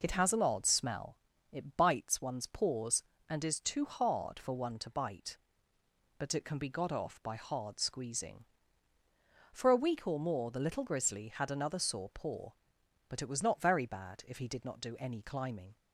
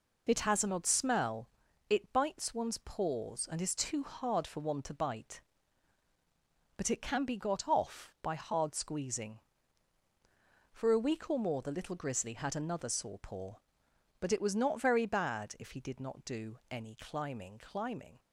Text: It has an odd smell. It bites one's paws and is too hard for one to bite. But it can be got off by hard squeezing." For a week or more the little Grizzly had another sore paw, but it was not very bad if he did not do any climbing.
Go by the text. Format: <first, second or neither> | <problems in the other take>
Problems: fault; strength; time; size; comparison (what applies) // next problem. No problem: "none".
first | says "climbing" twice; at 17.5 s